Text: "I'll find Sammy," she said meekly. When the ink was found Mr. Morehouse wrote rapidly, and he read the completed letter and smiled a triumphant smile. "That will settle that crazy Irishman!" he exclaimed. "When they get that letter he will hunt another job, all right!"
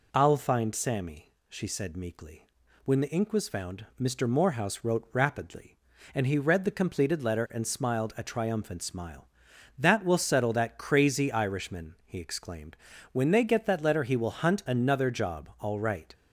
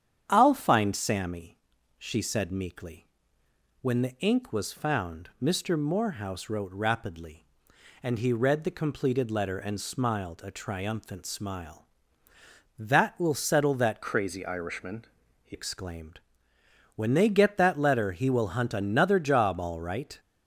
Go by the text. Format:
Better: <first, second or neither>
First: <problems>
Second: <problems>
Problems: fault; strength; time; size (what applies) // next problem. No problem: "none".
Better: first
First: none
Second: starts louder than the rest; strong; until 1.2 s; 8.5 dB // changes voice from "crazy" to "he"; from 14.0 to 15.5 s; 1.5 s long